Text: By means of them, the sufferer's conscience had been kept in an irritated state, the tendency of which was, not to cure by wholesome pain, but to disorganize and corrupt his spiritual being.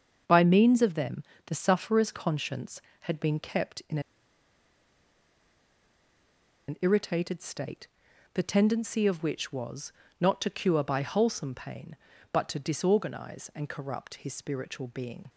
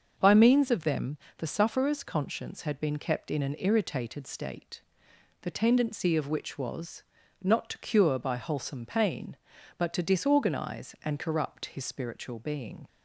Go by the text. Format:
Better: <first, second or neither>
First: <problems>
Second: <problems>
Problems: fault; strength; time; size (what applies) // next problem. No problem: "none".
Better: second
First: starts louder than the rest; until 1.5 s; 7 dB // pauses between "in" and "an"; strong; at 3.9 s; 2.6 s long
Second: starts louder than the rest; until 1.1 s; 6.5 dB